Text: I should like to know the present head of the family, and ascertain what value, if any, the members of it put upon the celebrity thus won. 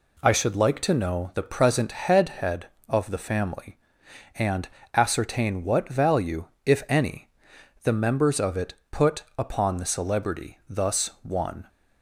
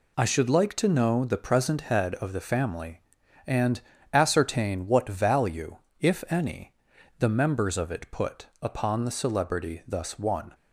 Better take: second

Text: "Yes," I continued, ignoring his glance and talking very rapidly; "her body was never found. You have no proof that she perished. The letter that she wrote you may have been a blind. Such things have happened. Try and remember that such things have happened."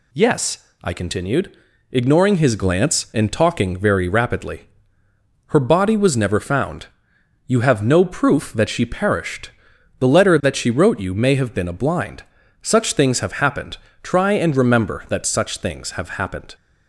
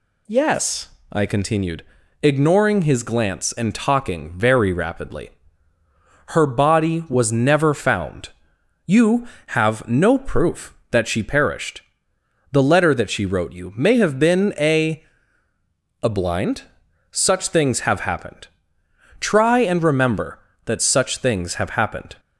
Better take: first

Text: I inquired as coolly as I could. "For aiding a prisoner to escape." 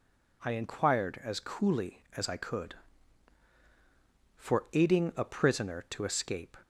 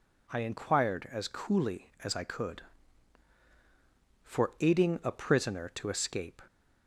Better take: neither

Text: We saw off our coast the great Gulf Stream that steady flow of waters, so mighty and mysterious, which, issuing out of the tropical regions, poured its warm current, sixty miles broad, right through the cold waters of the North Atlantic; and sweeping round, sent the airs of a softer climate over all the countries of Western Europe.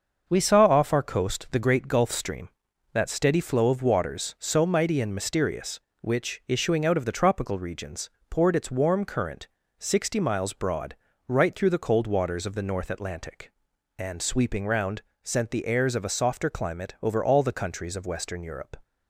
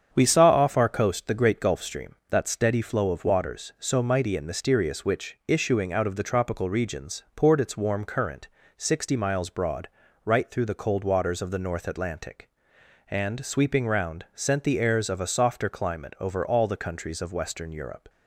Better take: neither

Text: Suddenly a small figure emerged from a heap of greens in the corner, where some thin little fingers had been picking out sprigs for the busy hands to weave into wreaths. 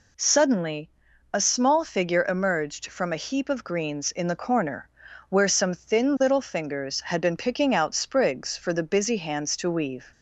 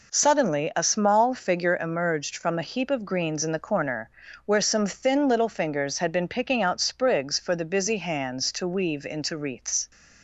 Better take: second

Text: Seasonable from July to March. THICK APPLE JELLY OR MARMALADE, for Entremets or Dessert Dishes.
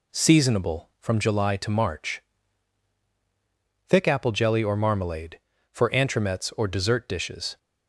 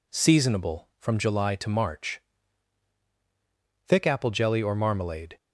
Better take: first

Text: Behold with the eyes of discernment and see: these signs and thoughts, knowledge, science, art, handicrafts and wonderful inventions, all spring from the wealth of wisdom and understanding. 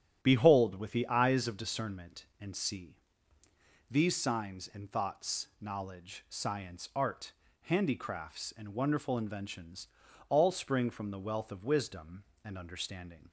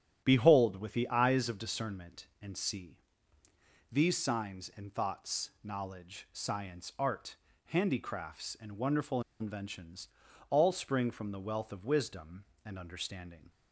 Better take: first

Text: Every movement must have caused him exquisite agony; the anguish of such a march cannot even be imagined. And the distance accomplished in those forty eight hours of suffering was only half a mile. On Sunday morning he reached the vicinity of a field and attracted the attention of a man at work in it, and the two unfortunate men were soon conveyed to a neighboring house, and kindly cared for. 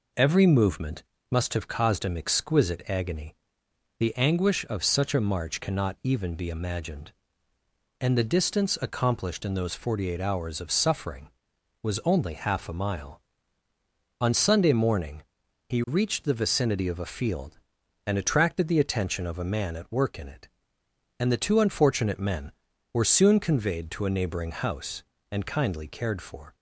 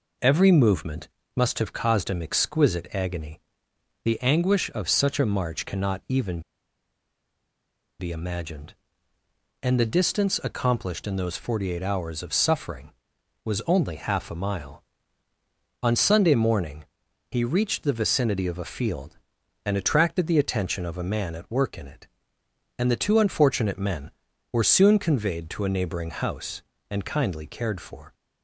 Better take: first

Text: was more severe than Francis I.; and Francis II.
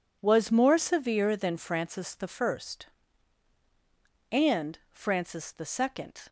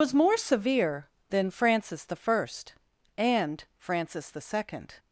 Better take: first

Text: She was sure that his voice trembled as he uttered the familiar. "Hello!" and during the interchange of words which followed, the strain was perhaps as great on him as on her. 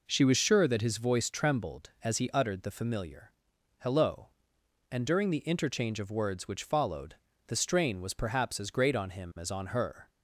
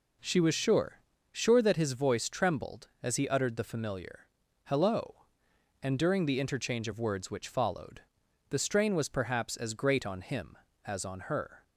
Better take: first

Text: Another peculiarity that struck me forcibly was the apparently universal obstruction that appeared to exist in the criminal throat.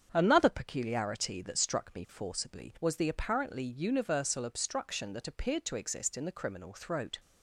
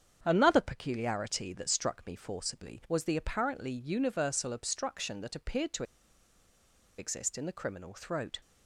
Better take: first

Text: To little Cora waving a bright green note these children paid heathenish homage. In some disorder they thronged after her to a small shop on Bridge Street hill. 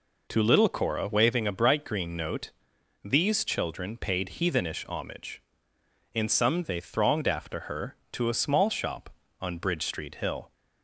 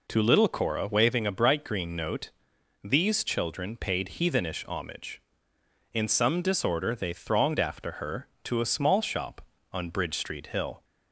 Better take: second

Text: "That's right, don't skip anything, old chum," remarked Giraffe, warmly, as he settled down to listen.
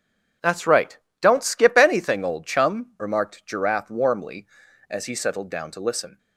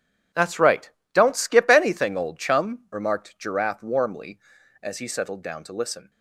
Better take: first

